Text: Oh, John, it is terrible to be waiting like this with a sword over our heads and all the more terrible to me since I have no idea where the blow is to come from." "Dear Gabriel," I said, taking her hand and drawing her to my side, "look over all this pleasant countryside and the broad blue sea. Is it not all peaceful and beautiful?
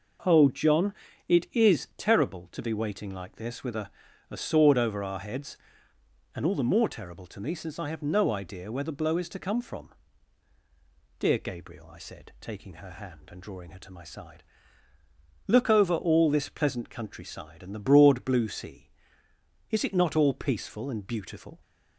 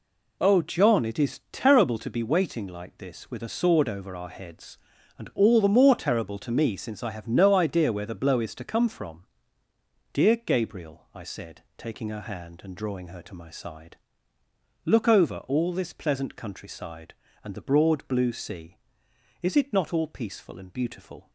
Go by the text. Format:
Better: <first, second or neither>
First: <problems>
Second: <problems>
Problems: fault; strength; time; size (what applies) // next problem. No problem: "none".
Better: second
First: says "a" twice; at 4.3 s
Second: none